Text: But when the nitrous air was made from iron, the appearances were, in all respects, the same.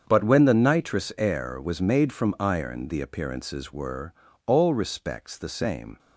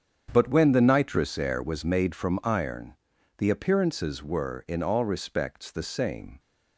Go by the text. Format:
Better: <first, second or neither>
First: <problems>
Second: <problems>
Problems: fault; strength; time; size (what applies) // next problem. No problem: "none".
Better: second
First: starts louder than the rest; strong; until 1.0 s; 7.5 dB // skips "in"; at 4.2 s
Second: starts louder than the rest; strong; until 1.3 s; 8 dB